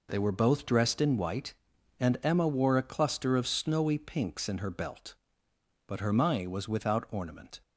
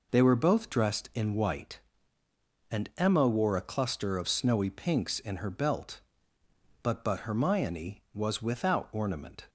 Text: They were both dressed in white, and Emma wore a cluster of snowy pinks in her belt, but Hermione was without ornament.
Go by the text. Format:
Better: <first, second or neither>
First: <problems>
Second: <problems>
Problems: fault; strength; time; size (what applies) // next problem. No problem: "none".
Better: first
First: none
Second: says "but" twice; at 7.0 s